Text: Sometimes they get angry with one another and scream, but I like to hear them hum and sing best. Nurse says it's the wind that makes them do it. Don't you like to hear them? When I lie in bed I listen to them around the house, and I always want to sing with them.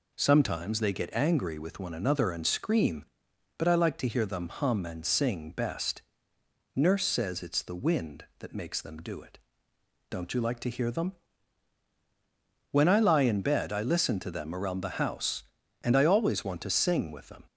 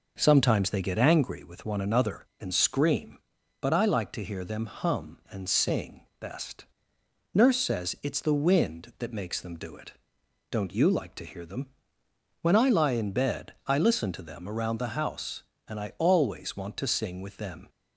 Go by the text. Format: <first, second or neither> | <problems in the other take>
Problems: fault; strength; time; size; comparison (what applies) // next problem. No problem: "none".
first | starts louder than the rest; noticeable; until 1.2 s; 5.5 dB